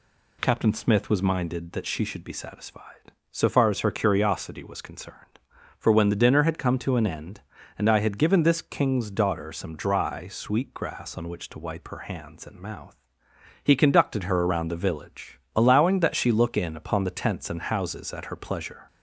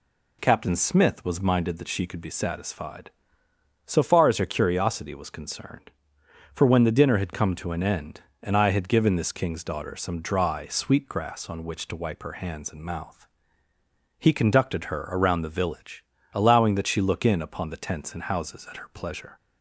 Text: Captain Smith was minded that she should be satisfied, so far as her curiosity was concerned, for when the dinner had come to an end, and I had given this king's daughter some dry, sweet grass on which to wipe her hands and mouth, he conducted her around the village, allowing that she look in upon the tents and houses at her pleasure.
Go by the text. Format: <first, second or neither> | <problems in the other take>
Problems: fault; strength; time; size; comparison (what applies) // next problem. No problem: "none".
first | says "could" for "should"; at 2.0 s